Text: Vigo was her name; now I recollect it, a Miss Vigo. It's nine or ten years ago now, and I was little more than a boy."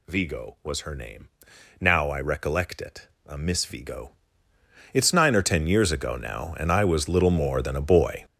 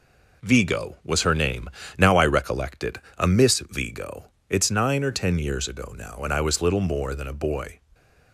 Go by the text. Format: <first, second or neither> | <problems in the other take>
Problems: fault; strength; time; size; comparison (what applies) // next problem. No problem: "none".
second | gets louder; strong; throughout; 11.5 dB